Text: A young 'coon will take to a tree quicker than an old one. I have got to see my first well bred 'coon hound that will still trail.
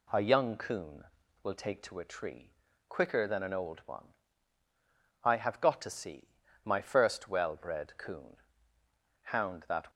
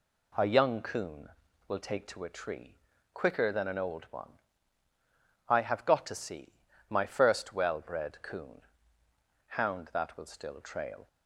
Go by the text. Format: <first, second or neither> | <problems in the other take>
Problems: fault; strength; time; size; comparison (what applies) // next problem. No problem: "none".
second | pauses between "tree" and "quicker"; slight; at 2.5 s; 0.34 s long; slight in the second // pauses between "see" and "my"; slight; at 6.2 s; 0.36 s long; slight in the second // pauses between "coon" and "hound"; noticeable; at 8.3 s; 0.86 s long; noticeable in the second // stops before "will still trail"; at 9.9 s